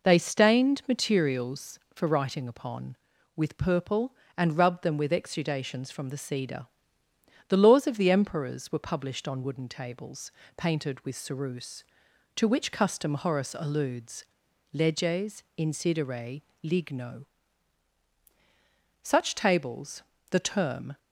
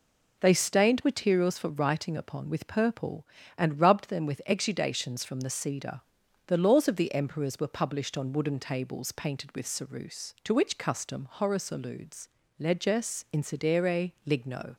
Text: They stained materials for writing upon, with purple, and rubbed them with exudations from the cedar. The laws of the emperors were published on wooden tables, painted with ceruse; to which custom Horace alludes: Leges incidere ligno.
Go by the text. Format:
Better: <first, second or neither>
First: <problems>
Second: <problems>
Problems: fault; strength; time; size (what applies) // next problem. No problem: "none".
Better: second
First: pauses between "incidere" and "ligno"; slight; at 16.4 s; 0.20 s long // goes on to say "Such tables the term"; strong; from 19.1 s on; 1.8 s long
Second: pauses between "incidere" and "ligno"; slight; at 14.1 s; 0.16 s long